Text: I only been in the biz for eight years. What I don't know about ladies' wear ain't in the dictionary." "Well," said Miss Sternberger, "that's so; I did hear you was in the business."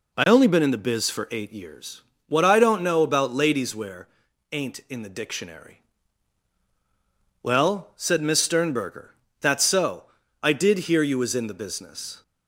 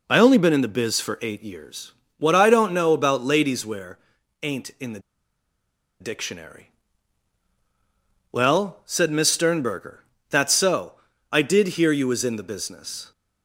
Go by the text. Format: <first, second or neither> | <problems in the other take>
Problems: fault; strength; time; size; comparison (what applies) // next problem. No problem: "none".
first | pauses between "wear" and "ain't"; at 3.9 s; 0.44 s long; also in the first // pauses between "the" and "dictionary"; at 4.9 s; 1.0 s long